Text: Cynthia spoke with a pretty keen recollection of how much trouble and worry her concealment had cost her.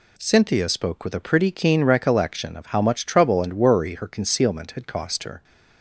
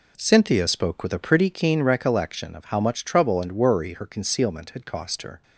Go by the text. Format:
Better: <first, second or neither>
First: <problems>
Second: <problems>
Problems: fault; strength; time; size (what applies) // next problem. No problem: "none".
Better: first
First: none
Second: starts louder than the rest; until 1.6 s; 3.5 dB